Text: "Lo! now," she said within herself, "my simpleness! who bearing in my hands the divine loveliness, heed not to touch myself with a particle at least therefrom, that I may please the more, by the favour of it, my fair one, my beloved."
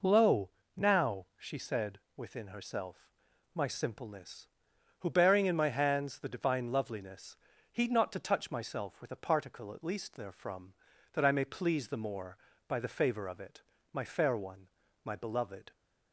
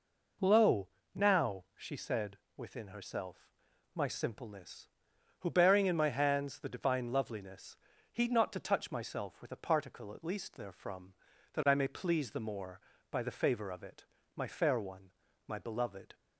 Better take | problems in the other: neither | pauses between "said" and "within"; slight; the same in both

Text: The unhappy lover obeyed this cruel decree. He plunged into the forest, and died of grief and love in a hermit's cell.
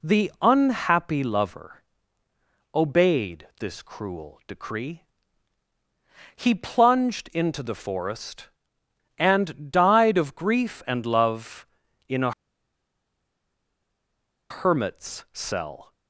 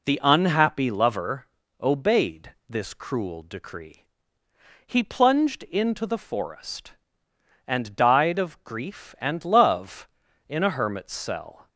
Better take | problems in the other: second | pauses between "lover" and "obeyed"; noticeable; at 1.8 s; 0.92 s long; slight in the second // pauses between "a" and "hermit's"; strong; at 12.3 s; 2.1 s long

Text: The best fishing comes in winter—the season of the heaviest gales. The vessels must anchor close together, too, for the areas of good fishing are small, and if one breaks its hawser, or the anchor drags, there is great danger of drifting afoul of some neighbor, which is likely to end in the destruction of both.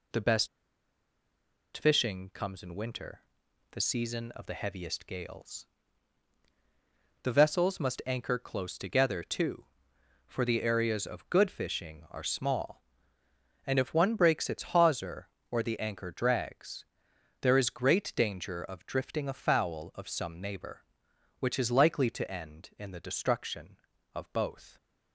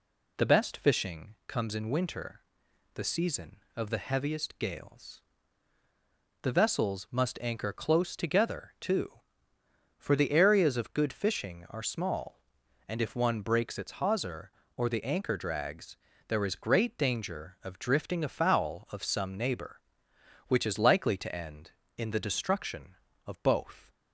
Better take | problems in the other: second | pauses between "best" and "fishing"; strong; at 0.4 s; 1.2 s long

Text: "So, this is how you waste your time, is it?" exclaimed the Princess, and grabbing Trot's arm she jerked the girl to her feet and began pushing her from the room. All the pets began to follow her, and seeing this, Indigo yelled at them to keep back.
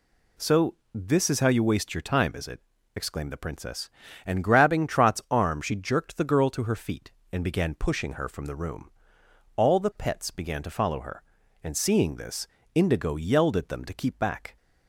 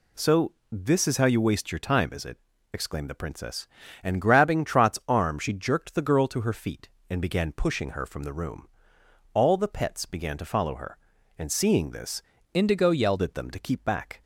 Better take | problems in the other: first | changes voice from "Indigo" to "yelled"; from 12.5 to 13.2 s; 0.7 s long

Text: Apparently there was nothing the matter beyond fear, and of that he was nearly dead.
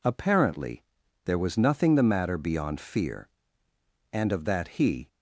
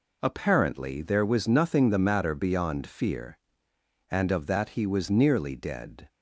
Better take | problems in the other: second | pauses between "Apparently" and "there"; at 0.8 s; 0.40 s long // stops before "was nearly dead"; at 5.0 s

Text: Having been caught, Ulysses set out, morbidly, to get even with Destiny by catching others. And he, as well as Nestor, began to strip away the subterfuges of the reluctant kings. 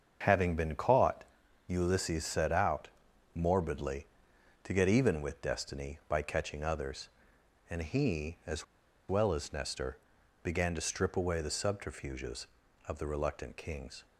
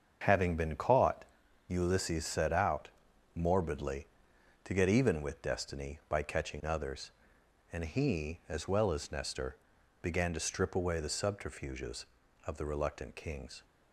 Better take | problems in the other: second | starts louder than the rest; until 1.6 s; 7 dB; also in the second // pauses between "as" and "well"; at 8.6 s; 0.44 s long

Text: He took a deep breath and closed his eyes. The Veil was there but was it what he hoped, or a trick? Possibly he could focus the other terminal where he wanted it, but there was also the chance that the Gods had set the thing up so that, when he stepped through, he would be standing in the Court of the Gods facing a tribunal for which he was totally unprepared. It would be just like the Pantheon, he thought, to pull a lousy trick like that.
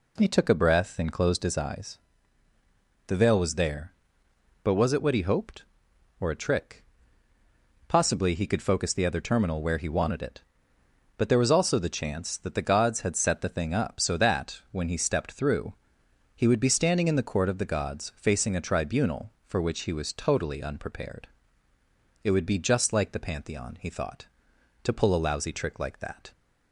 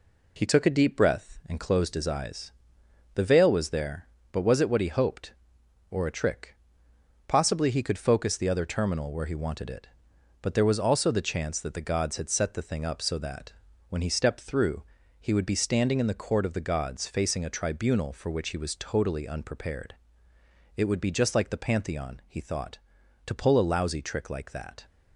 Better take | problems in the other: second | skips "deep"; at 0.5 s

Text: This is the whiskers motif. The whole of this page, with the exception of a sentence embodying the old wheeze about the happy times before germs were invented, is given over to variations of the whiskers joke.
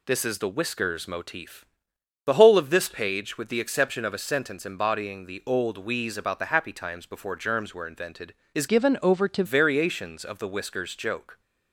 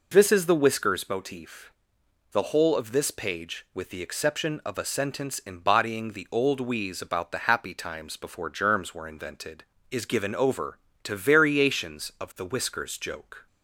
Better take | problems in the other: second | changes voice from "given" to "to"; from 8.6 to 9.4 s; 0.8 s long

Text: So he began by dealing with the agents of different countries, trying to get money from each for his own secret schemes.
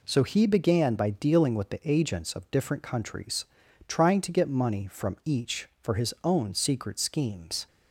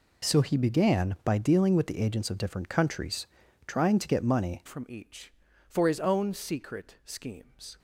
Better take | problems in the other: first | changes voice at "from"; from 4.6 s on; 3.1 s long

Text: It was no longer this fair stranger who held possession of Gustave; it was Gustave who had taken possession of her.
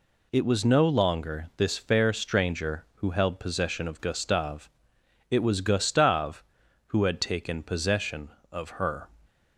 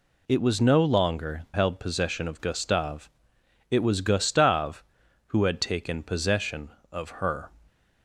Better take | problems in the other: first | skips "this fair stranger who"; at 1.4 s

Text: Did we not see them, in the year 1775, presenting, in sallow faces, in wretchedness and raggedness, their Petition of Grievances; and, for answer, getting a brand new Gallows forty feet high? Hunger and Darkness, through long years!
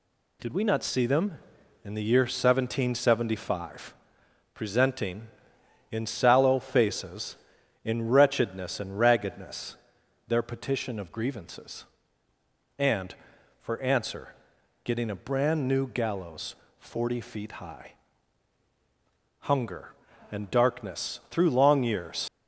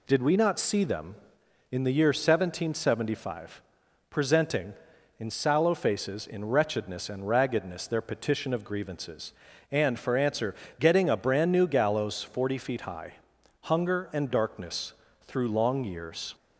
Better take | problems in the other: second | pauses between "Gallows" and "forty"; slight; at 16.5 s; 0.24 s long // leaves "years" unfinished; at 22.2 s; 75 ms

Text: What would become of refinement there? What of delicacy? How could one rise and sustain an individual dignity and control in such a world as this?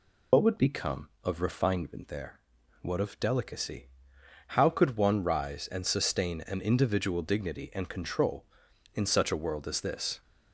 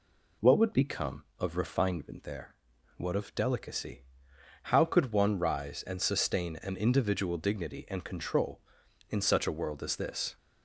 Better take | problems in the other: second | loses the start of "What"; at 0.3 s; 75 ms

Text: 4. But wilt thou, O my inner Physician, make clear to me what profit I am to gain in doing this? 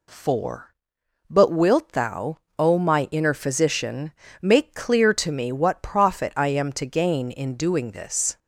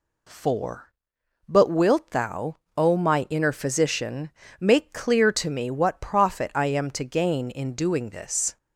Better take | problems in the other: neither | none

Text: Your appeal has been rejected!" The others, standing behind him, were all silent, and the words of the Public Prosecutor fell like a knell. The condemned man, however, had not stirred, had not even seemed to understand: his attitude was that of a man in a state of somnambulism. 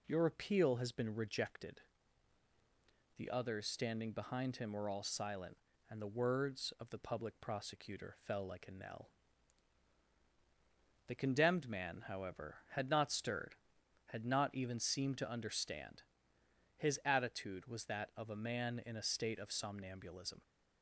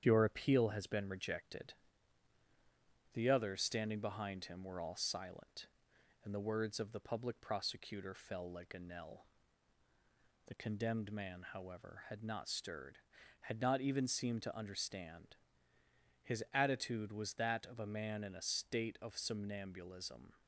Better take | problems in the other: first | gets quieter; slight; throughout; 3 dB

